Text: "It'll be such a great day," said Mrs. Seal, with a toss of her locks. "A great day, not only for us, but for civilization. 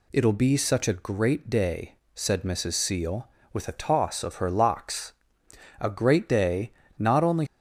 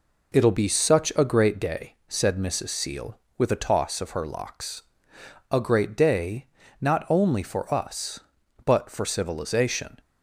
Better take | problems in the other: second | stops before "for us but for civilization"; at 7.4 s

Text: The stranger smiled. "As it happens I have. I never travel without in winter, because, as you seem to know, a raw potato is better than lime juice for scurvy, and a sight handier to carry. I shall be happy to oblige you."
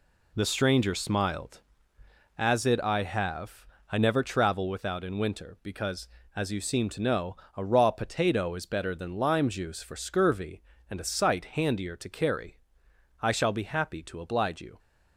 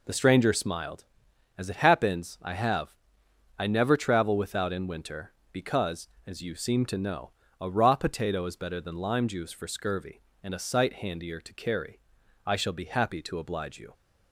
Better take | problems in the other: second | skips "happens"; at 2.8 s

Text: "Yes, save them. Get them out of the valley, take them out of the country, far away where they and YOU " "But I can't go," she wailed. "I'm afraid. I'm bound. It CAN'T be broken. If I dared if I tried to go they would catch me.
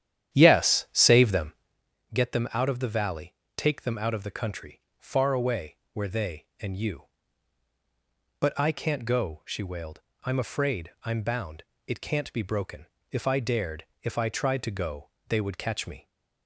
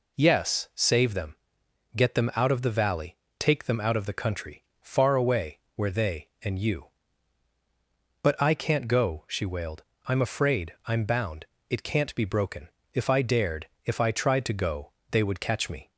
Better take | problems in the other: second | starts louder than the rest; strong; until 1.8 s; 11 dB // pauses between "away" and "where"; slight; at 5.7 s; 0.16 s long; slight in the second // pauses between "dared" and "if"; slight; at 13.8 s; 0.18 s long; slight in the second // pauses between "go" and "they"; slight; at 15.0 s; 0.22 s long; slight in the second

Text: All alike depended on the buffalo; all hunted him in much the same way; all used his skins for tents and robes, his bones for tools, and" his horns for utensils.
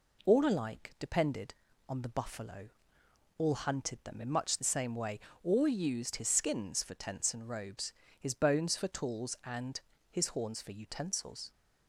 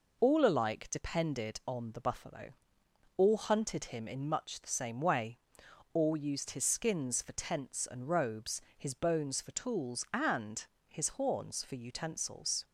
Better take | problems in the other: second | says "them" for "him"; at 4.0 s // pauses between "and" and "his"; slight; at 9.7 s; 0.30 s long; slight in the second

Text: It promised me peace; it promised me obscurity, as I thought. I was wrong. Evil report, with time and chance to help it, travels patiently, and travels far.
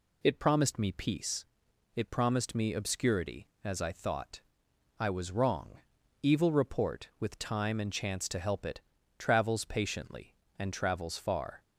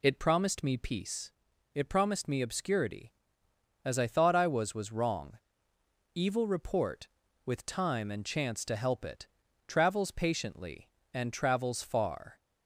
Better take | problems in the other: first | says "was" twice; at 4.7 s

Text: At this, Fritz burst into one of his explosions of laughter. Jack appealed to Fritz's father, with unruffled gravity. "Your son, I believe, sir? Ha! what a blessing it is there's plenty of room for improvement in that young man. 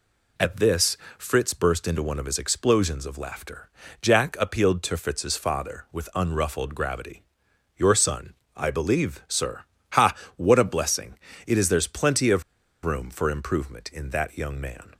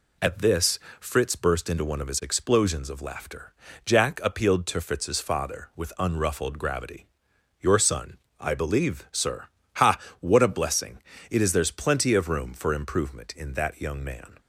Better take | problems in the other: second | pauses between "blessing" and "it"; slight; at 11.1 s; 0.32 s long; slight in the second // pauses between "of" and "room"; at 12.4 s; 0.41 s long

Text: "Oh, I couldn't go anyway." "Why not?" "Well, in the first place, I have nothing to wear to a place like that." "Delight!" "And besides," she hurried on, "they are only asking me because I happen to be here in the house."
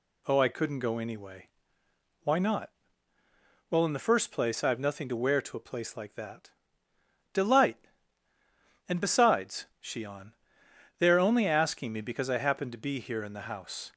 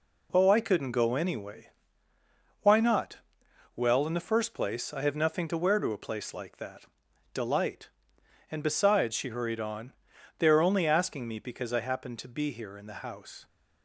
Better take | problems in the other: second | skips "hurried"; at 10.0 s

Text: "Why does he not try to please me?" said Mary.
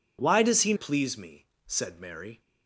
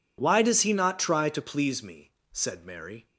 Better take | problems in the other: second | skips "not try to"; at 0.7 s

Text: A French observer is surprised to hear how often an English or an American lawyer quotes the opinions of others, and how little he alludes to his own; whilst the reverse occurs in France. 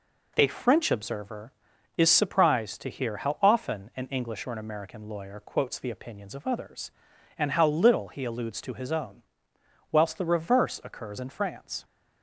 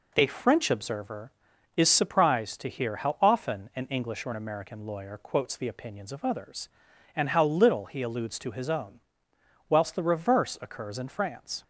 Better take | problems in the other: neither | none

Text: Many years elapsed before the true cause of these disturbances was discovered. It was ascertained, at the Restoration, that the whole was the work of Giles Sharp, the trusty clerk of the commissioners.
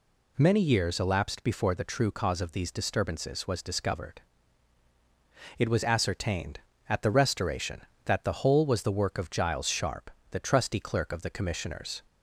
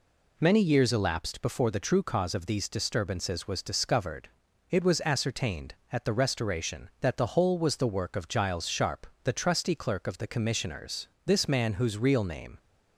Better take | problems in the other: first | goes on to say "This man whose real name"; from 11.2 s on; 1.3 s long

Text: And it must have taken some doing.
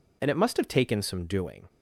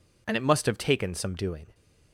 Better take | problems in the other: neither | none

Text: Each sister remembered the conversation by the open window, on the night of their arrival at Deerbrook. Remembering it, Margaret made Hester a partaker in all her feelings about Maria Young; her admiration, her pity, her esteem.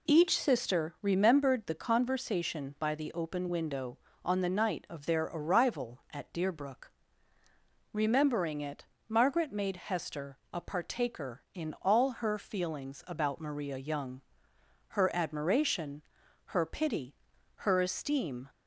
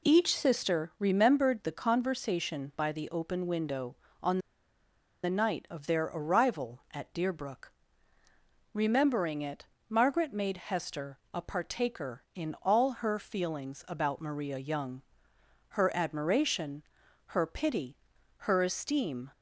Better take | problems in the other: first | pauses between "on" and "the"; noticeable; at 4.3 s; 0.84 s long // pauses between "Hester" and "a"; slight; at 11.1 s; 0.16 s long; slight in the first

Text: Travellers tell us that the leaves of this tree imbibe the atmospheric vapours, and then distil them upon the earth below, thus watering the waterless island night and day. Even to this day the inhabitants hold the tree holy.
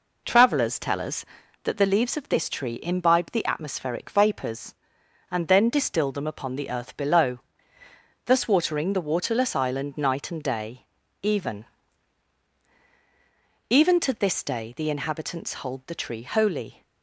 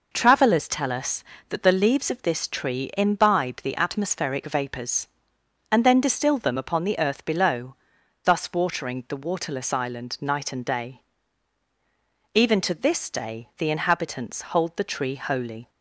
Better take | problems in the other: second | says "Even" twice; at 13.6 s

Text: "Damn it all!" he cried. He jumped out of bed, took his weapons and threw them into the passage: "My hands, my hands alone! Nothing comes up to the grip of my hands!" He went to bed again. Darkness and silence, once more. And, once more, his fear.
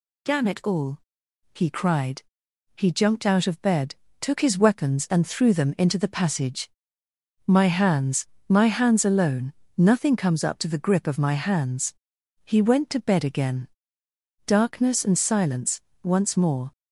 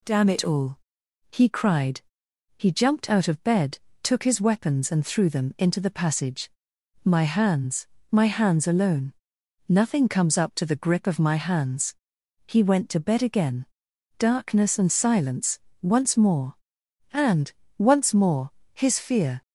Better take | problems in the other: second | stops before "And once more his fear"; at 16.7 s

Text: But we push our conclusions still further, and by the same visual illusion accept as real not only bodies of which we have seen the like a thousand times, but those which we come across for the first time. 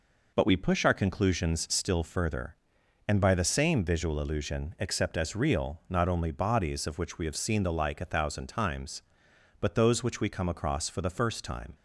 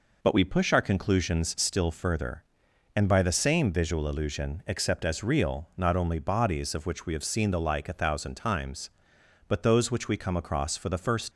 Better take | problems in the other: first | stops before "time"; at 11.3 s

